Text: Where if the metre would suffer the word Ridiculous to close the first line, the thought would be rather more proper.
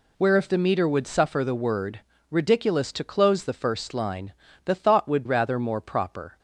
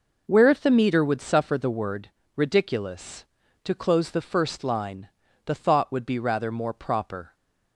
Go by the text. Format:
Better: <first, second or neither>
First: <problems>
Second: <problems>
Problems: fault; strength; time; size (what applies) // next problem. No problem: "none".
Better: second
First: pauses between "word" and "Ridiculous"; slight; at 1.9 s; 0.32 s long // skips "be"; at 5.2 s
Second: pauses between "word" and "Ridiculous"; slight; at 2.0 s; 0.26 s long